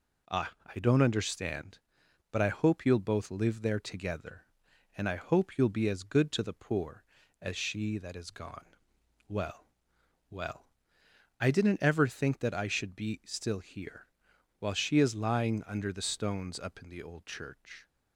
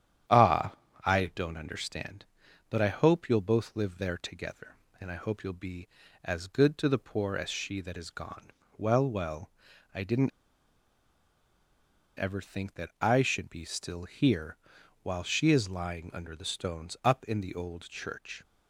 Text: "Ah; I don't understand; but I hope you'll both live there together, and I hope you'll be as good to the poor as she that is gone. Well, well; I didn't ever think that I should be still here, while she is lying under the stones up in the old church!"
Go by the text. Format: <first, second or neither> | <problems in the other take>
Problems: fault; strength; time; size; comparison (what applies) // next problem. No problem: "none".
first | starts louder than the rest; strong; until 1.6 s; 10 dB // pauses between "didn't" and "ever"; strong; at 10.3 s; 1.8 s long